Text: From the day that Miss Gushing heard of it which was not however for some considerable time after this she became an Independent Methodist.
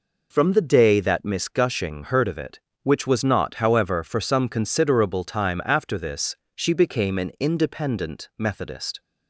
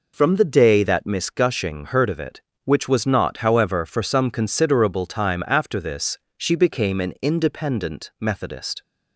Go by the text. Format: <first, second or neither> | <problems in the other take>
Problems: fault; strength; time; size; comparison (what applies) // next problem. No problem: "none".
neither | pauses between "this" and "she"; slight; the same in both